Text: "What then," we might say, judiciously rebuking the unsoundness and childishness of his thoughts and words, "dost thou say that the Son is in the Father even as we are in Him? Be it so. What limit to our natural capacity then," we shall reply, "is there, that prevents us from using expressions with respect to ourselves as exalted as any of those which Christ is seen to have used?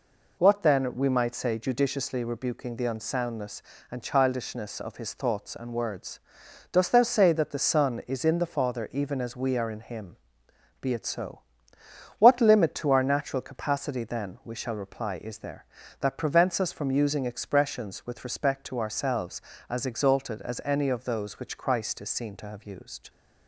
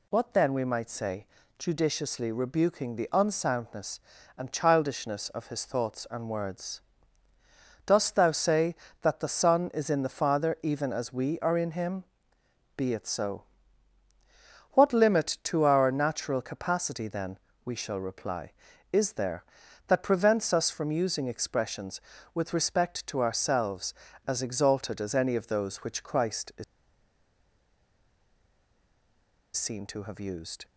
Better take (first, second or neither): first